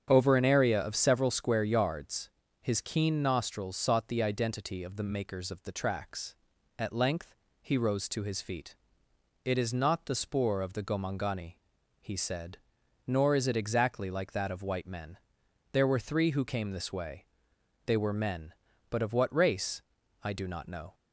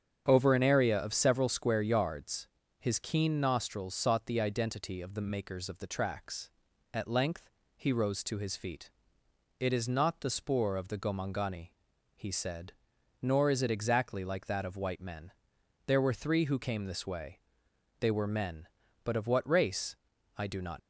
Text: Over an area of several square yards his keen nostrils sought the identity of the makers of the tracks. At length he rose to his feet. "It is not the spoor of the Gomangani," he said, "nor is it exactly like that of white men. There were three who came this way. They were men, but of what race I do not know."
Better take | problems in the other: first | starts louder than the rest; strong; until 1.2 s; 8.5 dB; strong in the first // pauses between "yards" and "his"; slight; at 2.4 s; 0.30 s long; slight in the first // pauses between "length" and "he"; slight; at 7.4 s; 0.28 s long; slight in the first // pauses between "race" and "I"; at 19.9 s; 0.42 s long; also in the first // stops before "know"; at 20.7 s

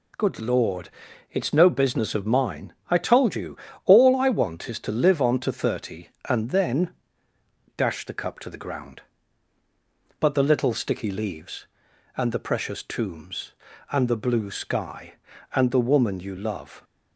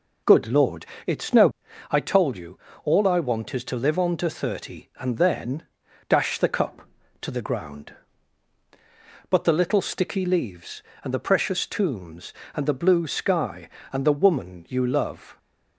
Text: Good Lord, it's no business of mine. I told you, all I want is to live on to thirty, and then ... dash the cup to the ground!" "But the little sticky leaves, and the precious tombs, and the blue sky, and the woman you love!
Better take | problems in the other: first | skips "business of mine"; at 1.6 s

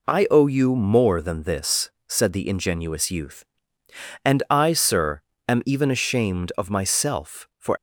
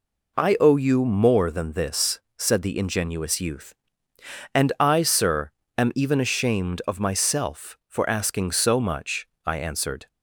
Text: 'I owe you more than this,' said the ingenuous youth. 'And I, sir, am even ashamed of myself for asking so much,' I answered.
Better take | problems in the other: second | stops before "asking so much I answered"; at 7.7 s

